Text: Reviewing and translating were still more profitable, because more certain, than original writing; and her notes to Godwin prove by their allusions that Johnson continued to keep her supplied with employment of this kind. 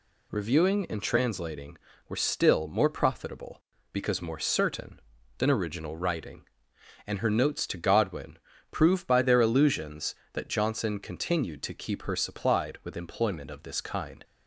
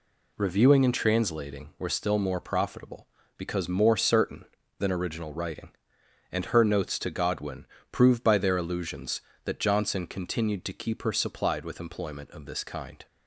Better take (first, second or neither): neither